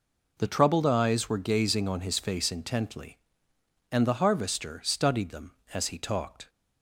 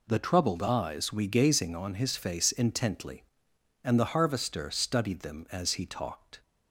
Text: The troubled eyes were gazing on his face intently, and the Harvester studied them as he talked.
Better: first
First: none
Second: says "we" for "were"; at 1.1 s

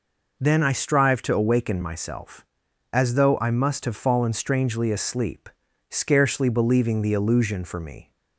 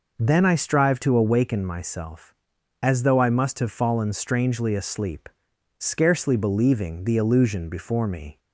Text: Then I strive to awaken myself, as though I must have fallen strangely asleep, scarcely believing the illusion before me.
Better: second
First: says "for" for "before"; at 7.6 s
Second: none

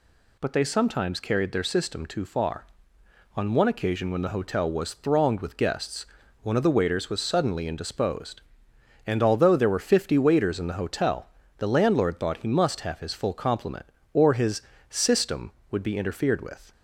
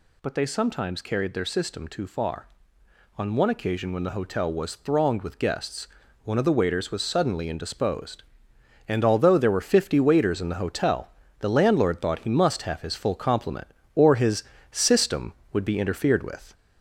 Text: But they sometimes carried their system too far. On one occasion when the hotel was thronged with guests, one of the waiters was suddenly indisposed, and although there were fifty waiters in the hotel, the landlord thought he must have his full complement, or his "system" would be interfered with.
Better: first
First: pauses between "his" and "system"; slight; at 14.6 s; 0.28 s long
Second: gets louder; slight; throughout; 3 dB // pauses between "his" and "system"; slight; at 14.4 s; 0.28 s long

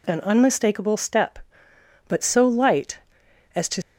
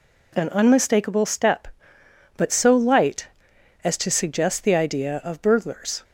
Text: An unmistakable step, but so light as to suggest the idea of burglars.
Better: second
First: stops before "suggest the idea of burglars"; at 3.8 s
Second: none

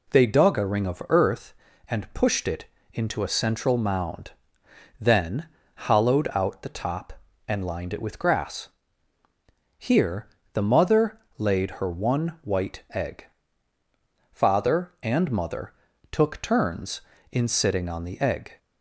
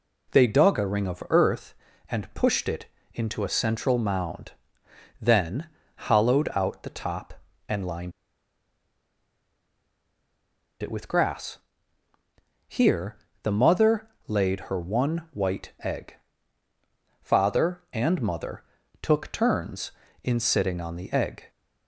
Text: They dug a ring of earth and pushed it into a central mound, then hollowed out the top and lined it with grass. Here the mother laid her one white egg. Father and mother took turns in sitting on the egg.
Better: first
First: pauses between "it" and "into"; slight; at 2.6 s; 0.28 s long // pauses between "then" and "hollowed"; slight; at 5.4 s; 0.28 s long // pauses between "Here" and "the"; slight; at 10.2 s; 0.28 s long // pauses between "mother" and "laid"; slight; at 11.1 s; 0.18 s long // pauses between "mother" and "took"; slight; at 15.7 s; 0.36 s long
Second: pauses between "it" and "into"; slight; at 2.8 s; 0.28 s long // pauses between "then" and "hollowed"; slight; at 5.6 s; 0.28 s long // pauses between "lined" and "it"; strong; at 8.1 s; 2.7 s long // pauses between "Here" and "the"; slight; at 13.1 s; 0.28 s long // pauses between "mother" and "laid"; slight; at 14.0 s; 0.18 s long // pauses between "mother" and "took"; slight; at 18.6 s; 0.36 s long

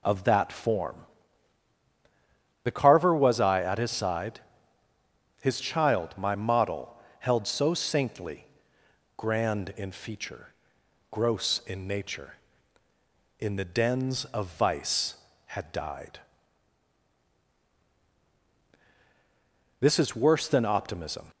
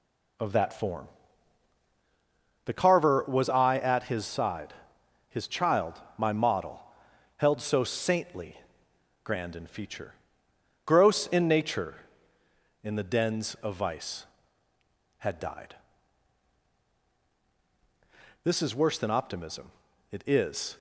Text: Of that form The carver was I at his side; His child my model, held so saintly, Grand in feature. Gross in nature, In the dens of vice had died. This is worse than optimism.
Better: first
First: pauses between "form" and "The"; strong; at 0.9 s; 1.6 s long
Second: pauses between "form" and "The"; strong; at 1.0 s; 1.5 s long // pauses between "child" and "my"; slight; at 5.9 s; 0.16 s long // goes on to say "It is"; noticeable; from 20.1 s on; 0.66 s long

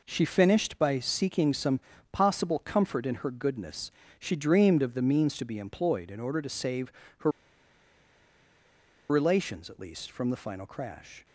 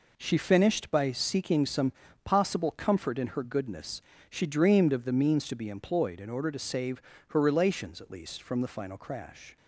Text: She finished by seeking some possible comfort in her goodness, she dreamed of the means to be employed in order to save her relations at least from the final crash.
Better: second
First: pauses between "some" and "possible"; slight; at 1.7 s; 0.32 s long // pauses between "save" and "her"; slight; at 6.9 s; 0.28 s long // pauses between "her" and "relations"; strong; at 7.3 s; 1.7 s long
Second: pauses between "some" and "possible"; slight; at 1.9 s; 0.32 s long // pauses between "save" and "her"; slight; at 7.0 s; 0.28 s long

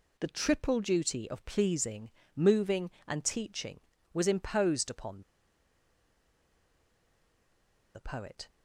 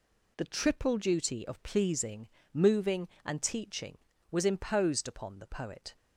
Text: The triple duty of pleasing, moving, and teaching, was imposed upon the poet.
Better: second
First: pauses between "upon" and "the"; strong; at 5.2 s; 2.7 s long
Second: none

